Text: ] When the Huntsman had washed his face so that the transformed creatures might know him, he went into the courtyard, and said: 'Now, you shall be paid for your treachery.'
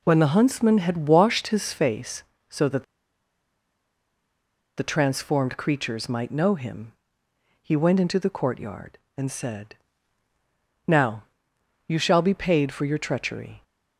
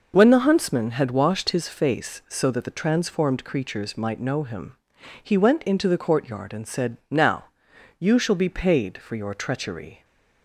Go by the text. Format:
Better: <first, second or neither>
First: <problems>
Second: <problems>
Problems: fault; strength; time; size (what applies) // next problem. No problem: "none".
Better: second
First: pauses between "that" and "the"; strong; at 2.8 s; 1.9 s long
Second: none